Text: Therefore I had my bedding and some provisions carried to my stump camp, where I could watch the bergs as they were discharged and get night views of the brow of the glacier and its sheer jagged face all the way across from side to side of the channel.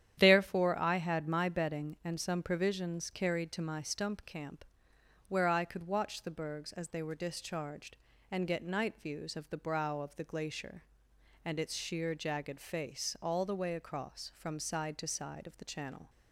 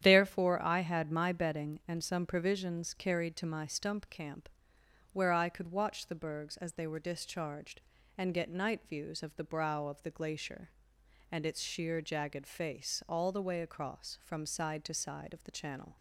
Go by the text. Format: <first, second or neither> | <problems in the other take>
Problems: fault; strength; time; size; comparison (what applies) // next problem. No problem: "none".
neither | starts louder than the rest; strong; the same in both